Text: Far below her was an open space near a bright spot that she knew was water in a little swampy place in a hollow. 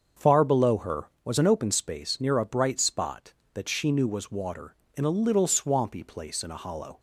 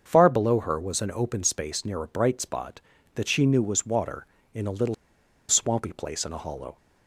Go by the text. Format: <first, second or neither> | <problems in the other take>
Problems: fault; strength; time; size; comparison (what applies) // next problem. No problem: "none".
first | starts louder than the rest; until 1.0 s; 6.5 dB; also in the first // pauses between "little" and "swampy"; noticeable; at 4.9 s; 0.54 s long